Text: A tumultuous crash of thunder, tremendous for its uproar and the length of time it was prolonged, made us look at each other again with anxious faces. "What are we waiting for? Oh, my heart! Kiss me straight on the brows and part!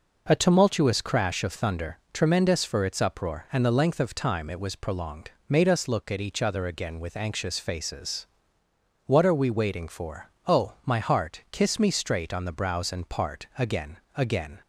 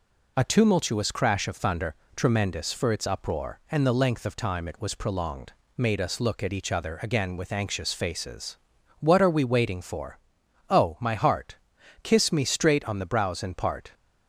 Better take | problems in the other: second | goes on to say "Again again"; noticeable; from 13.5 s on; 1.0 s long

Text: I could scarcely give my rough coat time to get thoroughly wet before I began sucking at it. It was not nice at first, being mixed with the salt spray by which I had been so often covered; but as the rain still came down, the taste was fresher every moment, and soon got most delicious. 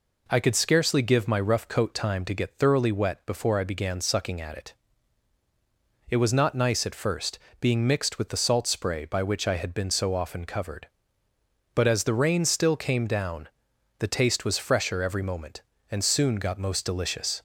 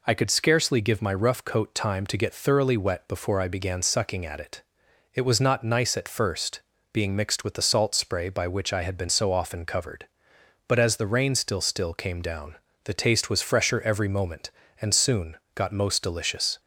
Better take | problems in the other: first | says "still" twice; at 11.6 s // pauses between "soon" and "got"; slight; at 15.3 s; 0.20 s long

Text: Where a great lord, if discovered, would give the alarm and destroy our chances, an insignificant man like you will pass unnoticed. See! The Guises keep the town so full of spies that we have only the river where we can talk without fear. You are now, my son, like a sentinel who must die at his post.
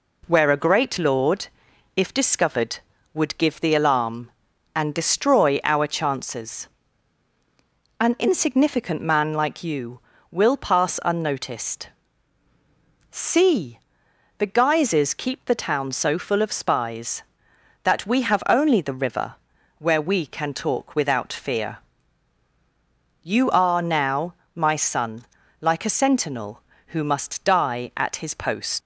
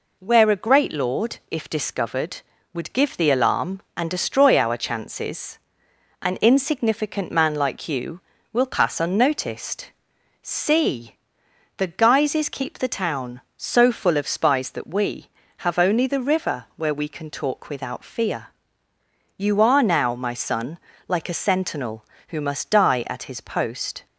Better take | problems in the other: second | pauses between "river" and "where"; at 19.3 s; 0.42 s long // leaves "post" unfinished; at 28.8 s; 115 ms

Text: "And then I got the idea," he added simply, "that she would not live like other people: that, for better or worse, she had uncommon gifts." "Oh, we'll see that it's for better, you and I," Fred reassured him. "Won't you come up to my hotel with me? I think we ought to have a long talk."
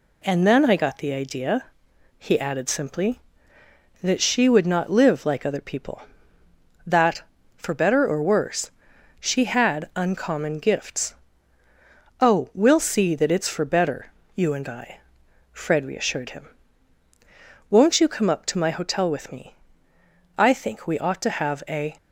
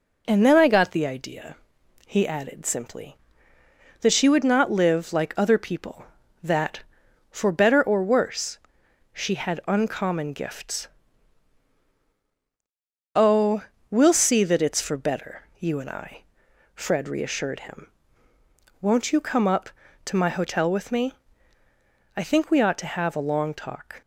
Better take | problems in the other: second | stops before "long talk"; at 21.9 s

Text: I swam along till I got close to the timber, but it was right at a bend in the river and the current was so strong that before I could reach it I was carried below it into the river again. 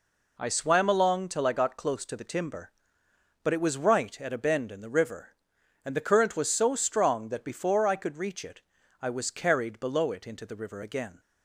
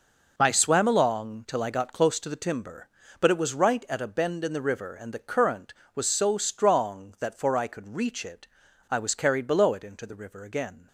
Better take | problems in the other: first | says "for" for "before"; at 7.3 s // pauses between "it" and "I"; at 8.4 s; 0.43 s long; also in the first

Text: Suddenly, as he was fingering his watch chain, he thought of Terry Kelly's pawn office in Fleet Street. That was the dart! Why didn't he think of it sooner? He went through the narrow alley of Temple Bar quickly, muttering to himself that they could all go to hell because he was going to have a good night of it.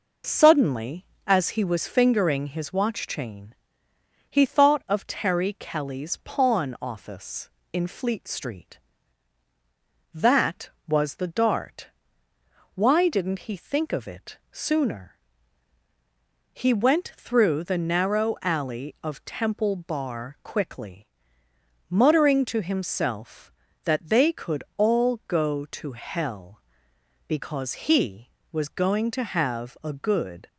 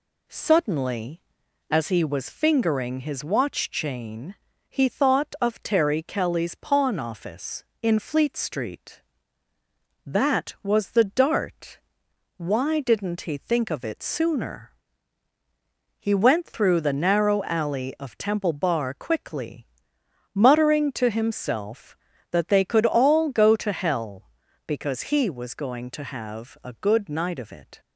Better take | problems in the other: second | stops before "night of it"; at 30.4 s

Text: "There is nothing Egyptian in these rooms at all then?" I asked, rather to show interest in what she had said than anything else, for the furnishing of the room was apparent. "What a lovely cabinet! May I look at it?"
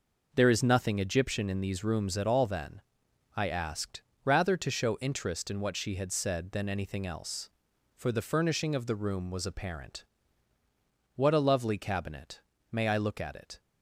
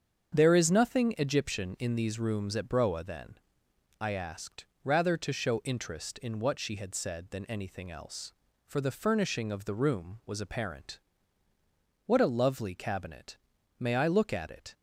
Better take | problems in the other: first | starts louder than the rest; strong; until 1.4 s; 7.5 dB // says "broa" for "all"; at 2.6 s

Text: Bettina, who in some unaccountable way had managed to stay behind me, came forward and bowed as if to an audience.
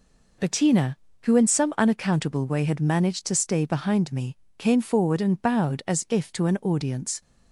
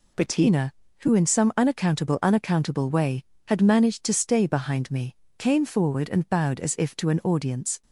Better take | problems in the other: first | says "unaccountable" twice; at 2.2 s

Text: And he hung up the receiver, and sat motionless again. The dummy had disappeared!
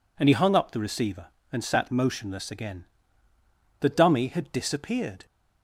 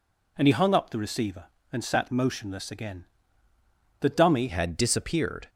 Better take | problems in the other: first | changes voice at "had"; from 4.4 s on; 1.0 s long

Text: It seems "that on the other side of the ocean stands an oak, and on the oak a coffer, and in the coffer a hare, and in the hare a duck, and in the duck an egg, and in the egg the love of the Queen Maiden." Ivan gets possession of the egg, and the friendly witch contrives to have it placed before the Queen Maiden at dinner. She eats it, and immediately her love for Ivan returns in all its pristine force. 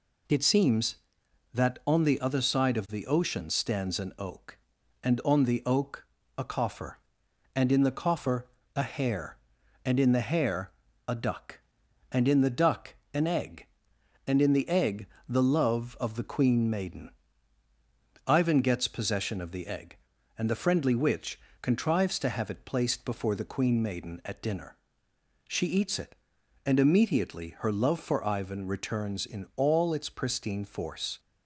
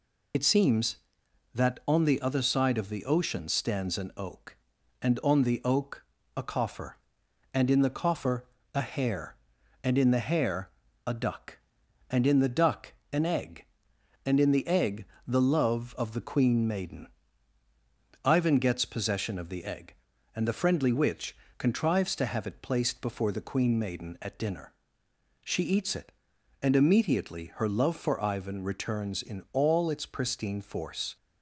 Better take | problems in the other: first | loses the start of "It"; at 0.3 s; 70 ms // pauses between "oak" and "a"; slight; at 6.0 s; 0.32 s long; slight in the first // pauses between "coffer" and "a"; slight; at 8.4 s; 0.30 s long; slight in the first // pauses between "hare" and "a"; slight; at 10.6 s; 0.36 s long; slight in the first // pauses between "duck" and "an"; slight; at 12.9 s; 0.20 s long; slight in the first // pauses between "egg" and "the"; slight; at 15.0 s; 0.22 s long; slight in the first // pauses between "witch" and "contrives"; slight; at 21.3 s; 0.22 s long; slight in the first

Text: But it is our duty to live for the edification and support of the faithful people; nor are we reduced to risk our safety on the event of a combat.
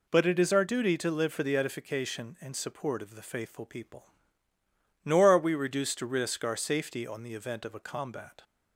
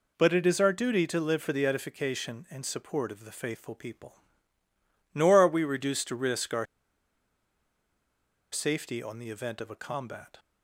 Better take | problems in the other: first | pauses between "our" and "safety"; strong; at 6.6 s; 1.8 s long

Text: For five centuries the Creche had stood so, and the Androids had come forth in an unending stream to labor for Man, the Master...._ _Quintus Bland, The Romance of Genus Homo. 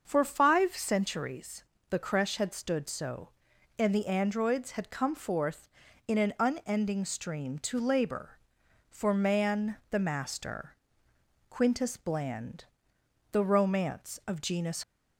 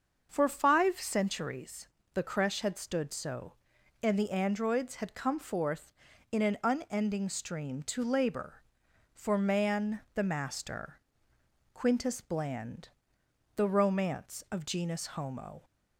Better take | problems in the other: second | starts louder than the rest; until 1.0 s; 6.5 dB; also in the second // pauses between "centuries" and "the"; slight; at 1.6 s; 0.26 s long; slight in the second // stops before "Homo"; at 14.8 s

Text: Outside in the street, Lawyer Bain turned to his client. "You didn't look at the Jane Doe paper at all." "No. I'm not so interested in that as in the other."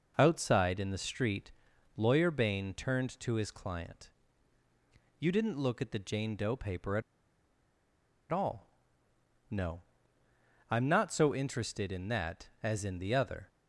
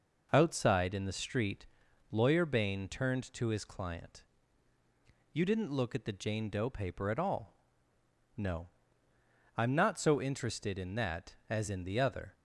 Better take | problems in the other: second | pauses between "at" and "all"; strong; at 7.0 s; 1.2 s long

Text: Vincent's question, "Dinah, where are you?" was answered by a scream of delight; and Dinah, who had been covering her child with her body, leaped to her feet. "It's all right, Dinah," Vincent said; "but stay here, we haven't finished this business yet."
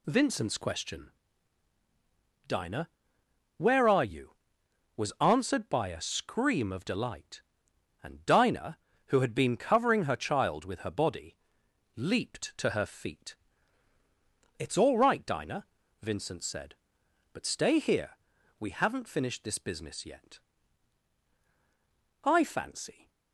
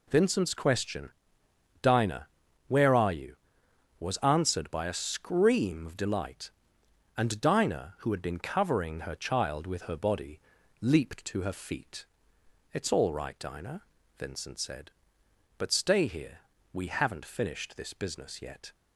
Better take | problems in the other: second | goes on to say "I fancy"; noticeable; from 22.2 s on; 0.86 s long

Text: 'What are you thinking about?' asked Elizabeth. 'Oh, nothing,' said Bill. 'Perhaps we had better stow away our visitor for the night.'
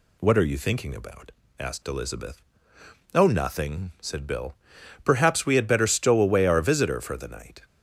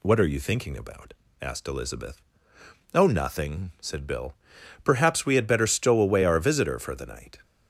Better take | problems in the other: neither | none

